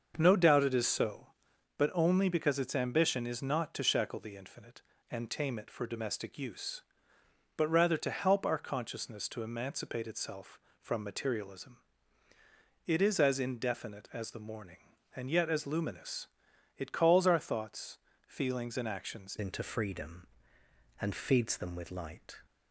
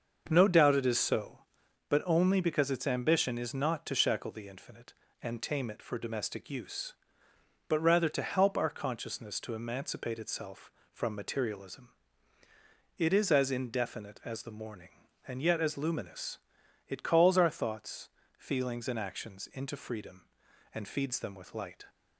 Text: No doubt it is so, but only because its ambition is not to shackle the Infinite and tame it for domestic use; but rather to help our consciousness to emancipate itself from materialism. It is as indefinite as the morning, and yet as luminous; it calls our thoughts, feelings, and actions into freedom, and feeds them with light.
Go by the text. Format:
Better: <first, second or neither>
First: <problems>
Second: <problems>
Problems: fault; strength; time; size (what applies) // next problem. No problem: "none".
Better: second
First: starts louder than the rest; until 1.1 s; 6.5 dB // changes voice at "into"; from 19.3 s on; 3.1 s long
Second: starts louder than the rest; until 1.2 s; 6.5 dB